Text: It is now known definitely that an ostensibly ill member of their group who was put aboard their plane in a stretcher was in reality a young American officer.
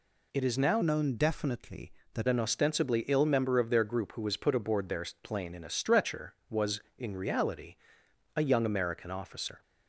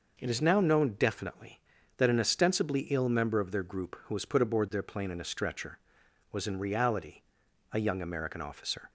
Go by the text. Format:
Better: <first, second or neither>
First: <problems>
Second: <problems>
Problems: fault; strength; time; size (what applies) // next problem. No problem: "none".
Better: second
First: changes voice from "known" to "that"; from 0.8 to 2.2 s; 1.4 s long // pauses between "their" and "plane"; slight; at 5.0 s; 0.16 s long // pauses between "reality" and "a"; noticeable; at 7.7 s; 0.60 s long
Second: pauses between "reality" and "a"; noticeable; at 7.2 s; 0.50 s long